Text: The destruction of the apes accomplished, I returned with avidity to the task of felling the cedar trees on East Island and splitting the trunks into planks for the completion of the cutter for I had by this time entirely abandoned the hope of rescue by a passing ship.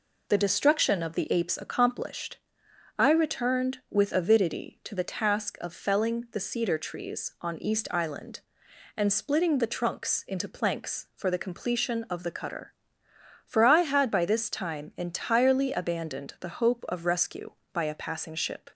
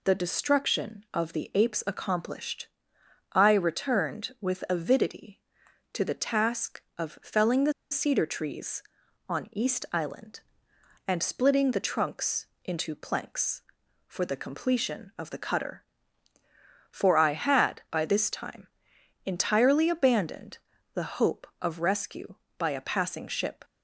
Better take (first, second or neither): first